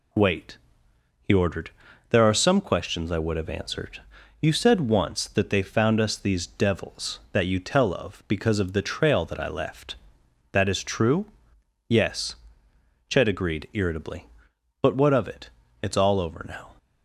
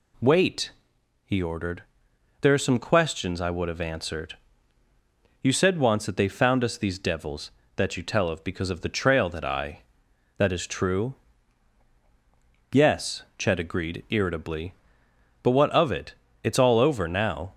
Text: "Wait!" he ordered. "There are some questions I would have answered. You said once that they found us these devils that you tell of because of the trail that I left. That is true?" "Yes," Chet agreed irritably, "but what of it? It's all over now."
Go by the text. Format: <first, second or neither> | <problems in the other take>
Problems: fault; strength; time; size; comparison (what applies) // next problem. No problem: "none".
first | skips "left"; at 10.0 s